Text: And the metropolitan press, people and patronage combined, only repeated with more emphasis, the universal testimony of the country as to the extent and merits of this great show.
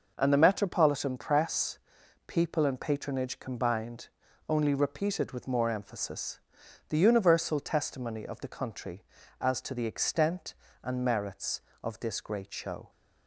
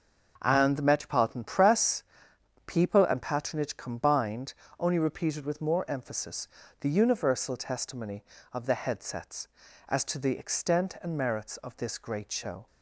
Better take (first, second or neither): first